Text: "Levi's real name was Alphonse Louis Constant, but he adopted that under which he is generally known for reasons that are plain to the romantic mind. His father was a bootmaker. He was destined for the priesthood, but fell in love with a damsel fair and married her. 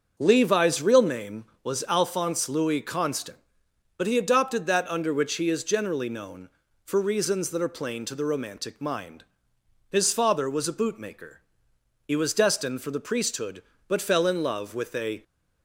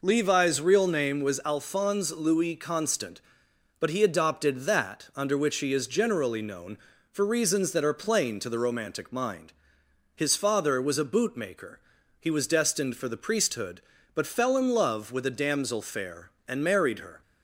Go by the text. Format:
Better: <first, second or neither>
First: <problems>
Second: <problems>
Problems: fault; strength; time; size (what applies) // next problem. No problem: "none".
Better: second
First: starts louder than the rest; until 1.1 s; 6.5 dB // stops before "damsel fair and married her"; at 15.2 s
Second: none